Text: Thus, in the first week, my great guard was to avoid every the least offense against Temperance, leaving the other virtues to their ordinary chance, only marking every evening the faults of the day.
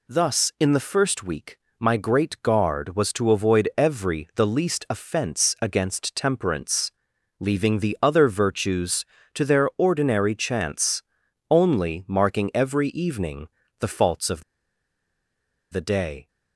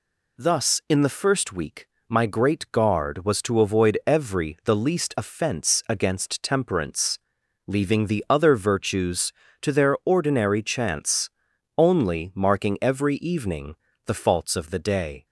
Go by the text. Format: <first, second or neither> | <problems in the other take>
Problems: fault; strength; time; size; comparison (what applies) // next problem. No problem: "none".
second | pauses between "evening" and "the"; slight; at 13.4 s; 0.32 s long; slight in the second // pauses between "of" and "the"; strong; at 14.4 s; 1.2 s long